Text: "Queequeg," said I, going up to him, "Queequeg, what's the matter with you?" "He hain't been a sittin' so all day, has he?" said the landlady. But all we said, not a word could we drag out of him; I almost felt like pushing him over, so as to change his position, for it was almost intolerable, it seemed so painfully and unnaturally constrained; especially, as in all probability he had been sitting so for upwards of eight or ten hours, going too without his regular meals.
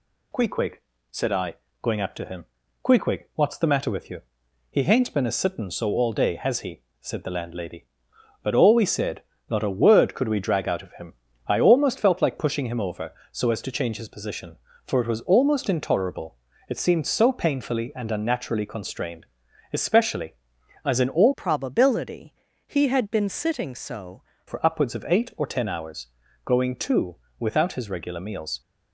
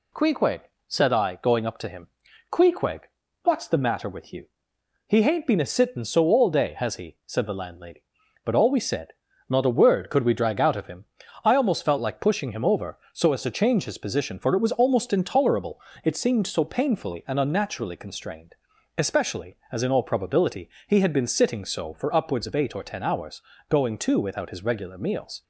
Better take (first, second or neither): second